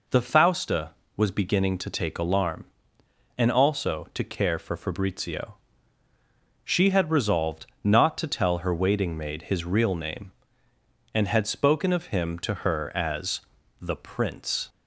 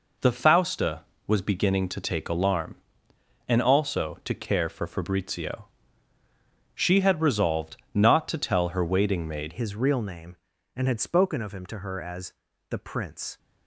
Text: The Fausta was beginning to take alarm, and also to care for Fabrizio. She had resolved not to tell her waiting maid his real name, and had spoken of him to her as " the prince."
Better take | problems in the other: first | pauses between "resolved" and "not"; slight; at 7.7 s; 0.18 s long; slight in the first // changes voice at "his"; from 9.5 s on; 3.8 s long

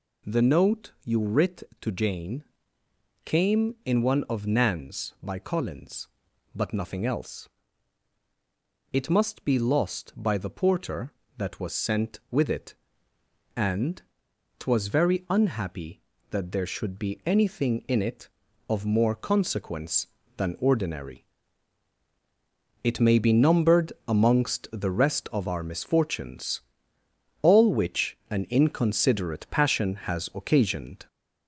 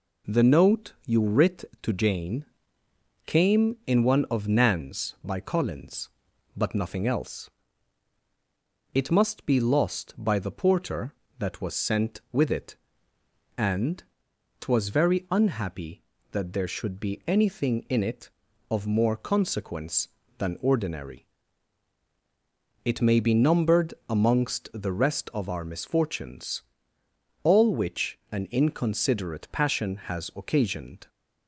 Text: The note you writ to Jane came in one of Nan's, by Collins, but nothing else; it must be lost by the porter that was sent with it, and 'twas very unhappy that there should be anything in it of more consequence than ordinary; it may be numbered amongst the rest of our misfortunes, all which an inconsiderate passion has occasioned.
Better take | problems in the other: second | gets louder; throughout; 3.5 dB // pauses between "Jane" and "came"; noticeable; at 2.4 s; 0.82 s long; noticeable in the second // pauses between "and" and "twas"; noticeable; at 14.0 s; 0.56 s long; noticeable in the second // pauses between "numbered" and "amongst"; slight; at 23.9 s; 0.16 s long; slight in the second

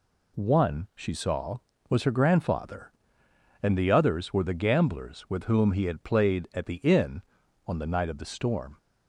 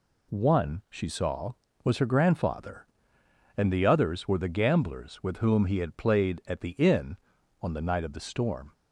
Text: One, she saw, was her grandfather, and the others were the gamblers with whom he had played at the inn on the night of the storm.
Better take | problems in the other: neither | none

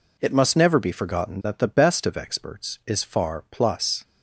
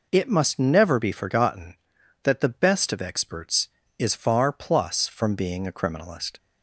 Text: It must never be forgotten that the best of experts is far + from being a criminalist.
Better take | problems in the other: second | stops before "from being a criminalist"; at 4.0 s

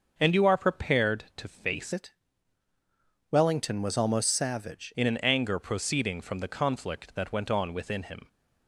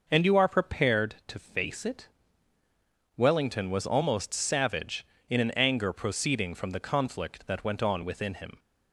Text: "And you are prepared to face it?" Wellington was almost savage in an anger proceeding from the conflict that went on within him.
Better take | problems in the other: second | starts louder than the rest; until 1.1 s; 6.5 dB // changes voice from "it" to "savage"; from 1.9 to 4.9 s; 3.0 s long

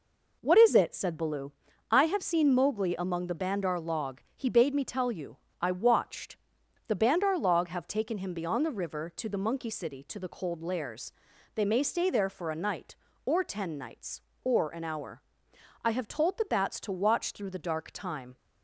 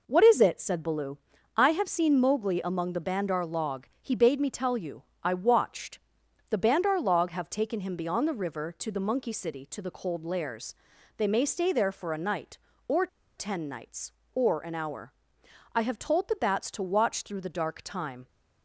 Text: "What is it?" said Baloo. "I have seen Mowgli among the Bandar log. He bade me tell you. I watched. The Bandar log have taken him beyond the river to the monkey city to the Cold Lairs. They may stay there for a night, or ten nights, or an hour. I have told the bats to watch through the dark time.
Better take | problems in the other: first | pauses between "or" and "ten"; slight; at 13.0 s; 0.30 s long

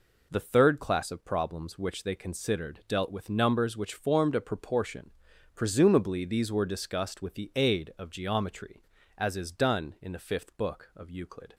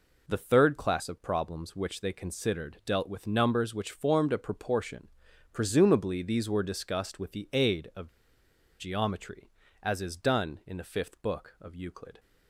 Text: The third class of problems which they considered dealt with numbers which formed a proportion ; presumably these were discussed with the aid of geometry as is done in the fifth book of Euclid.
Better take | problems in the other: first | pauses between "of" and "geometry"; noticeable; at 8.0 s; 0.71 s long

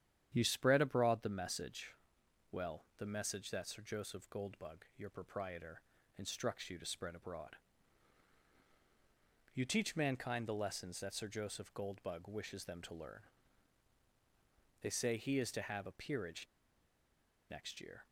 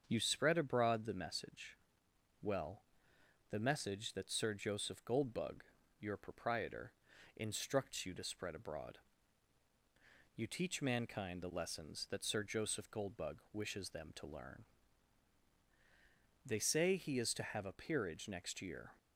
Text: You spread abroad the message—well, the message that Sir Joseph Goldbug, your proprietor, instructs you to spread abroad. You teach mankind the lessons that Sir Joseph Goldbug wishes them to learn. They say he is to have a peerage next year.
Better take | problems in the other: second | starts louder than the rest; strong; until 1.3 s; 9.5 dB; also in the second // pauses between "peerage" and "next"; at 16.4 s; 1.0 s long

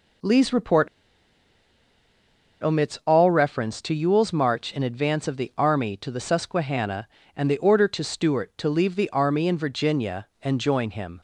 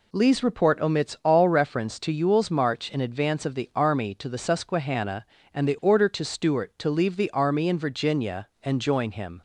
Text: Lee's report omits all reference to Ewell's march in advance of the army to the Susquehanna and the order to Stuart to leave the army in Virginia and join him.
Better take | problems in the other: second | pauses between "report" and "omits"; strong; at 0.8 s; 1.7 s long

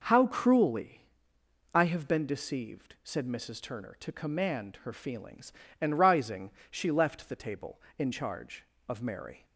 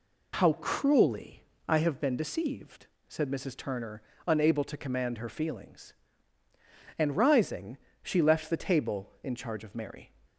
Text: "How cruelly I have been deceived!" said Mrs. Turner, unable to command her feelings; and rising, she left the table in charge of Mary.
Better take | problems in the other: second | pauses between "cruelly" and "I"; noticeable; at 1.0 s; 0.70 s long; slight in the second // skips "unable"; at 3.9 s

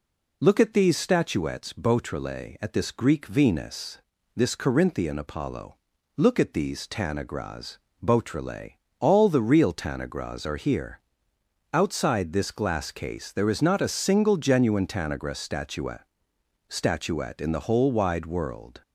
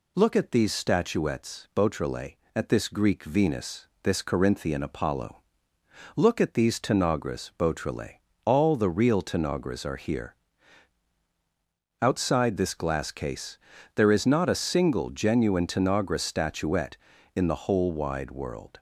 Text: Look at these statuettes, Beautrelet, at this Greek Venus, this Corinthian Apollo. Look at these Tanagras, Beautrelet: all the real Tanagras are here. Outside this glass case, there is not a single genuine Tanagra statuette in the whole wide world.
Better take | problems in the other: second | says "statuette" twice; at 16.6 s

